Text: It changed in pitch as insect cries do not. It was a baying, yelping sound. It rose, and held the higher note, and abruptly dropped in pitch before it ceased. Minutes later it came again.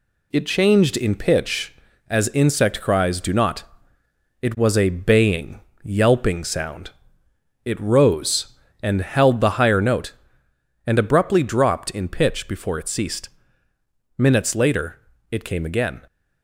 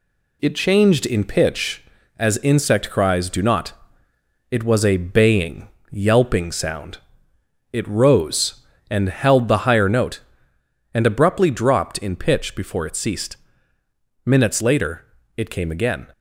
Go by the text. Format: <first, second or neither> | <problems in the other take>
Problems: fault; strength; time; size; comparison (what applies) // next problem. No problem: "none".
neither | pauses between "later" and "it"; slight; the same in both